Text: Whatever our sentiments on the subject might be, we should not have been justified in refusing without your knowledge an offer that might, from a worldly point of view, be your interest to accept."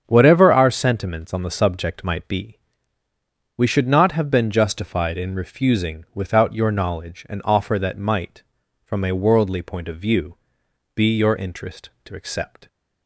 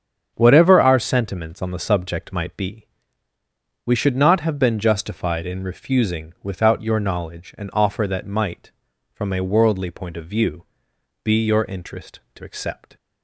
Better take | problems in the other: neither | starts louder than the rest; strong; the same in both

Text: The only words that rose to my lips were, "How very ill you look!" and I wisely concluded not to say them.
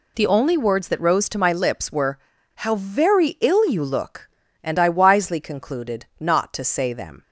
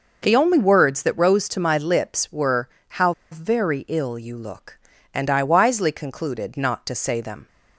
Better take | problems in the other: first | pauses between "How" and "very"; slight; at 3.1 s; 0.20 s long

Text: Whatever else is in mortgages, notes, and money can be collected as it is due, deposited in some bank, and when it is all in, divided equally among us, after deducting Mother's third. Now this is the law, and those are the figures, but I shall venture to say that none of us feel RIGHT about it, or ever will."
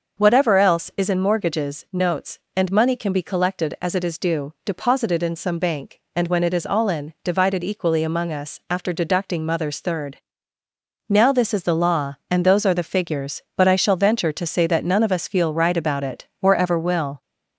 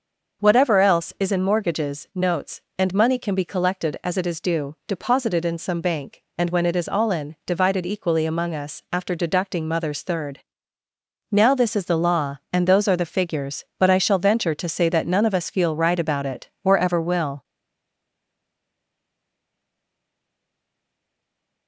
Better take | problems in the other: first | starts louder than the rest; until 1.5 s; 6.5 dB; also in the first // stays silent after the last word; strong; from 17.4 s on; 4.2 s long

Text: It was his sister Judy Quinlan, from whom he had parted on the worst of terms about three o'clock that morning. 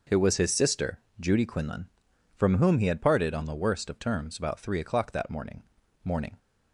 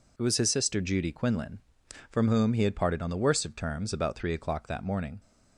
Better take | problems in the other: second | pauses between "sister" and "Judy"; slight; at 0.9 s; 0.20 s long // says "morning" twice; at 6.0 s

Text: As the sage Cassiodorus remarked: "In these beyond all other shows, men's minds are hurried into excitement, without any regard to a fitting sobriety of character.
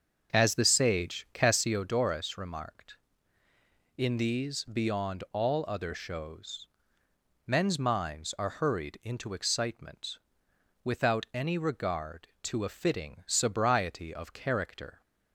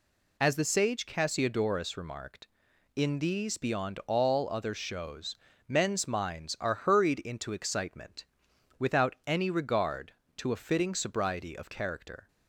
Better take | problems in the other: second | starts louder than the rest; until 1.9 s; 6.5 dB

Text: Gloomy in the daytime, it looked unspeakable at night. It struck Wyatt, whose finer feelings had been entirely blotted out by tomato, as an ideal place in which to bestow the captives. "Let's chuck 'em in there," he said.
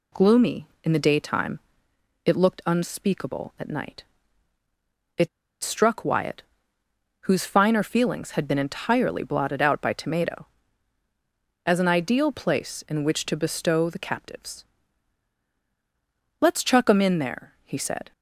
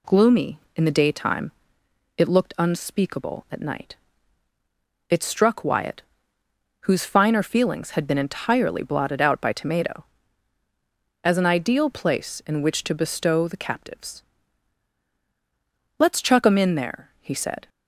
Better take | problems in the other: second | pauses between "It" and "struck"; slight; at 5.2 s; 0.35 s long

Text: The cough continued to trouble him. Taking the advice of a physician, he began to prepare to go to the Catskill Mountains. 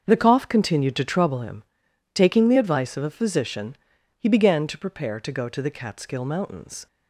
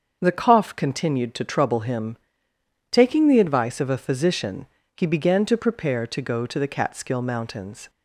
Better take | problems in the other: neither | starts louder than the rest; the same in both

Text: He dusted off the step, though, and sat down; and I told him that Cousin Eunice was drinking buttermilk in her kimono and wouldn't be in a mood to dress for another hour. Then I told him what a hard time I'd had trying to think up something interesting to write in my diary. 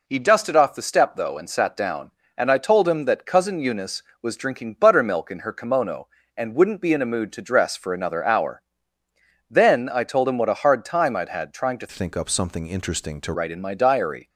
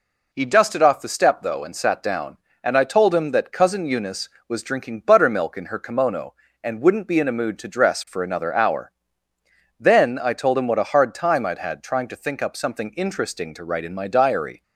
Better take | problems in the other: second | changes voice from "think" to "to"; from 11.8 to 13.3 s; 1.5 s long

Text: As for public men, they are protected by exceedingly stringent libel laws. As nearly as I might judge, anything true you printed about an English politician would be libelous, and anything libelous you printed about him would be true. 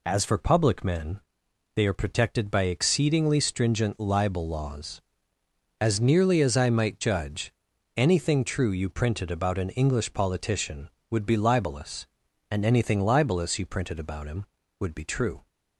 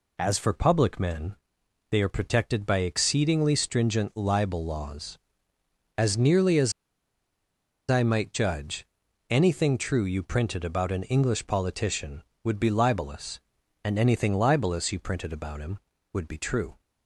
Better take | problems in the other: first | pauses between "as" and "I"; at 6.7 s; 1.1 s long

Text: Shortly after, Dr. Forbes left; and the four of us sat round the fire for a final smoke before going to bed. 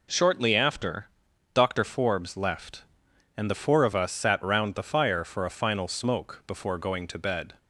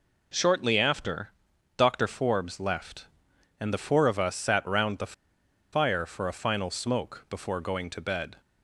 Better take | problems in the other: first | pauses between "the" and "fire"; noticeable; at 5.1 s; 0.60 s long

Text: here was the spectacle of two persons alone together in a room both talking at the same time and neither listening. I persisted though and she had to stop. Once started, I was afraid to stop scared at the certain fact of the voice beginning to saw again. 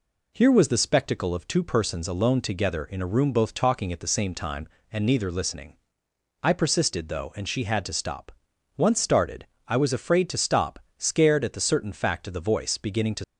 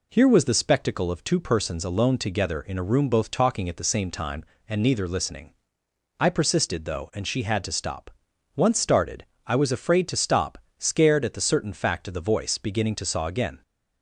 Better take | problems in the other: second | pauses between "stop" and "scared"; slight; at 10.7 s; 0.18 s long; slight in the second // stops before "saw again"; at 13.2 s

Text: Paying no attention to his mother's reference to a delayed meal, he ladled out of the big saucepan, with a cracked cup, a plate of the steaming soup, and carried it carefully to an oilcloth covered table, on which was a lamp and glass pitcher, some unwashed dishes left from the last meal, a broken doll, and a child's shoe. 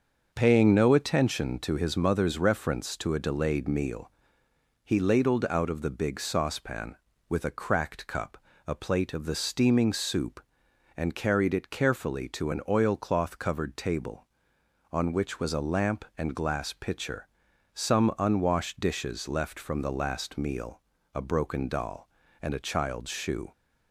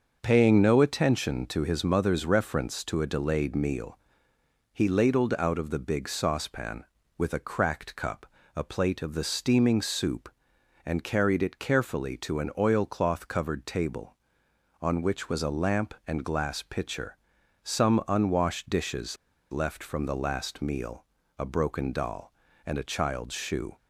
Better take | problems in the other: first | starts louder than the rest; noticeable; until 1.2 s; 6 dB; noticeable in the first // pauses between "dishes" and "left"; slight; at 19.1 s; 0.35 s long

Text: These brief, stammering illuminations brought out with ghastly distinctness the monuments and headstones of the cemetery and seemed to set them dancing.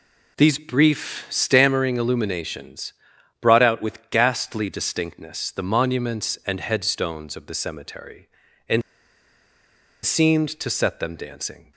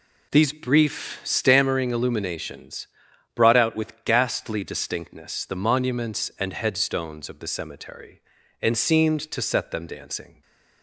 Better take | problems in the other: second | pauses between "illuminations" and "brought"; noticeable; at 2.9 s; 0.48 s long; noticeable in the second // pauses between "and" and "seemed"; at 8.8 s; 1.2 s long

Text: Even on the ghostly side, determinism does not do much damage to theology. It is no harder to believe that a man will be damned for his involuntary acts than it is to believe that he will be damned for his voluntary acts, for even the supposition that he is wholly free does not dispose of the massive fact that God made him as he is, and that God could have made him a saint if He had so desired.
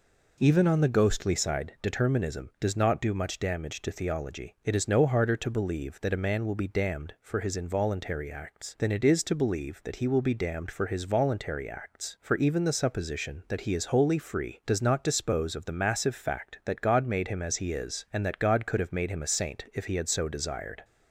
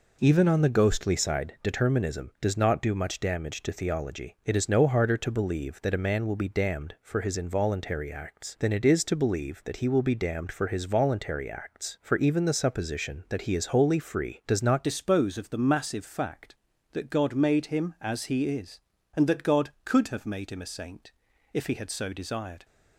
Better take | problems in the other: first | changes voice at "dispose"; from 14.8 s on; 7.8 s long // pauses between "saint" and "if"; at 21.1 s; 0.42 s long

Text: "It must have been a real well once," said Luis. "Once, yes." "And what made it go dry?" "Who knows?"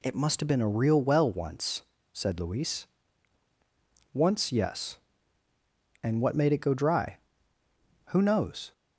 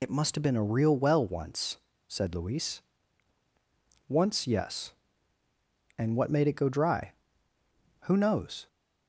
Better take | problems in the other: first | loses the start of "It"; at 0.0 s; 55 ms

